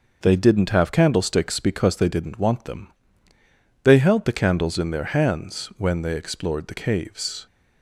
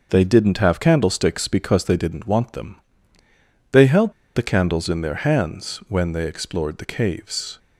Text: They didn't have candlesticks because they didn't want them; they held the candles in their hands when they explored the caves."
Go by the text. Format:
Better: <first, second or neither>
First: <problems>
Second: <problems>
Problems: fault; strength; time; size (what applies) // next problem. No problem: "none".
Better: first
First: none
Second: starts louder than the rest; noticeable; until 1.1 s; 6 dB // pauses between "held" and "the"; slight; at 4.1 s; 0.23 s long